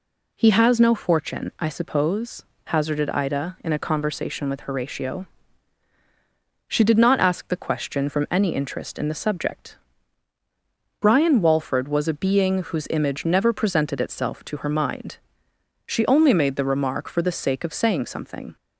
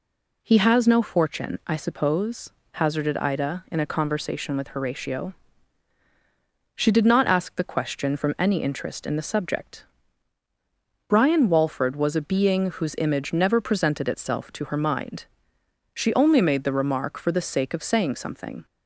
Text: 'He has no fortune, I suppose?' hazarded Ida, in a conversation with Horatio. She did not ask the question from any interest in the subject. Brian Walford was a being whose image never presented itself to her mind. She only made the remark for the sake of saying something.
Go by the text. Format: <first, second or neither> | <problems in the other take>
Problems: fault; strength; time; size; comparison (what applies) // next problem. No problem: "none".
neither | none